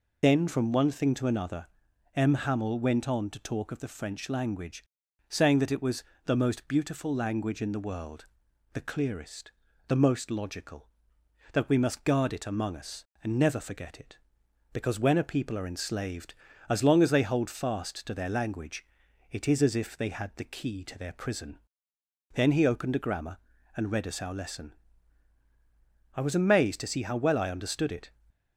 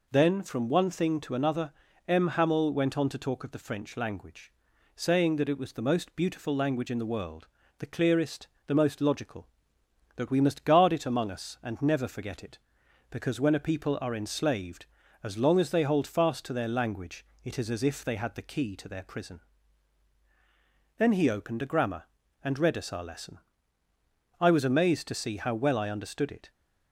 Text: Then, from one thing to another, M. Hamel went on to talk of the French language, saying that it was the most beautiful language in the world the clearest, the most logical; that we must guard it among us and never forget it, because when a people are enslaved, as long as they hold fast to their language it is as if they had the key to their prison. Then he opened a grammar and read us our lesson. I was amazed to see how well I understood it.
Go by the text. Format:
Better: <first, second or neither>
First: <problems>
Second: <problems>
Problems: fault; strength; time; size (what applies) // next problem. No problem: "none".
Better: second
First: loses the start of "Then"; at 0.2 s; 45 ms // pauses between "was" and "the"; slight; at 6.0 s; 0.22 s long // pauses between "world" and "the"; noticeable; at 8.2 s; 0.48 s long // pauses between "language" and "it"; at 18.8 s; 0.44 s long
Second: pauses between "world" and "the"; slight; at 7.4 s; 0.32 s long // pauses between "language" and "it"; slight; at 17.2 s; 0.18 s long